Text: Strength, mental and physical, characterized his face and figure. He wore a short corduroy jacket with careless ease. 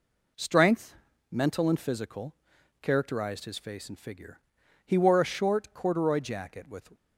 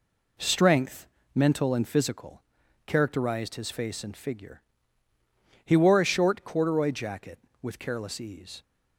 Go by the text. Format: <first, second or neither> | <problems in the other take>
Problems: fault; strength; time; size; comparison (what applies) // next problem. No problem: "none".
second | stops before "careless ease"; at 6.9 s